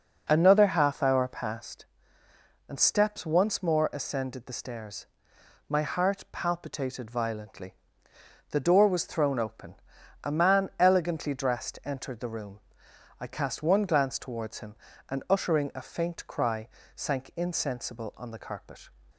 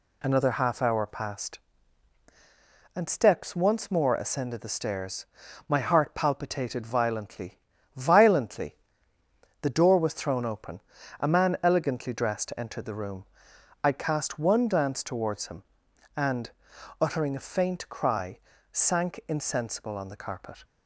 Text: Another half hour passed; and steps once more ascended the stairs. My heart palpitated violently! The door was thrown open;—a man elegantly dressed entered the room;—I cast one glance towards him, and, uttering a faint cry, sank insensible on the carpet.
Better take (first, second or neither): first